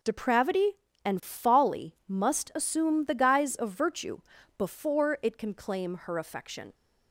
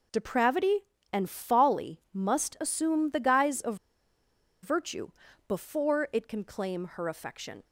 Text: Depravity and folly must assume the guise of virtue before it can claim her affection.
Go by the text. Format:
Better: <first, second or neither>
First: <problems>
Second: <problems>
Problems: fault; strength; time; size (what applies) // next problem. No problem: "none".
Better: first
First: pauses between "virtue" and "before"; at 4.1 s; 0.40 s long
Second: pauses between "of" and "virtue"; noticeable; at 3.7 s; 0.87 s long // pauses between "virtue" and "before"; at 5.0 s; 0.40 s long